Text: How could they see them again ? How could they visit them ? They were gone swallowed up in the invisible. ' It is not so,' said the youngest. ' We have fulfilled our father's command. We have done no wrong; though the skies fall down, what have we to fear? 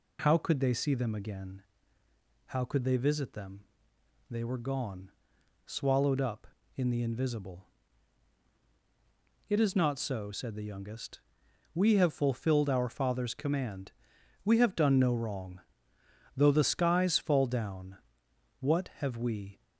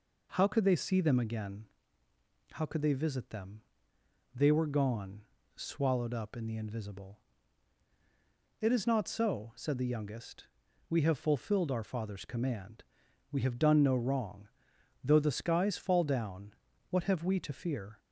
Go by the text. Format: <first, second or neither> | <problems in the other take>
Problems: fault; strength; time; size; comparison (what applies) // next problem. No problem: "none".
second | pauses between "gone" and "swallowed"; noticeable; at 5.0 s; 0.56 s long; slight in the second // stops before "to fear"; at 19.6 s